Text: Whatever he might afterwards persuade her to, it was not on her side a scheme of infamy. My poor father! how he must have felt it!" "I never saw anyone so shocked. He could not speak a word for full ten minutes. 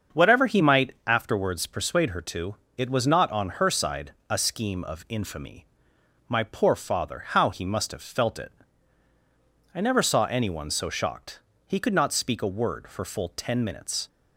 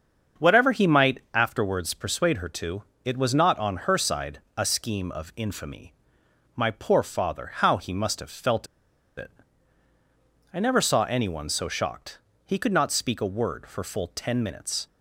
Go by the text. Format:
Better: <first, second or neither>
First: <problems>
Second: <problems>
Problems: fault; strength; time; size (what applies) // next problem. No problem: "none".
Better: first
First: starts louder than the rest; until 1.2 s; 7 dB // pauses between "side" and "a"; slight; at 4.1 s; 0.18 s long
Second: starts louder than the rest; until 1.5 s; 7 dB // pauses between "side" and "a"; slight; at 4.3 s; 0.18 s long // pauses between "felt" and "it"; noticeable; at 8.6 s; 0.51 s long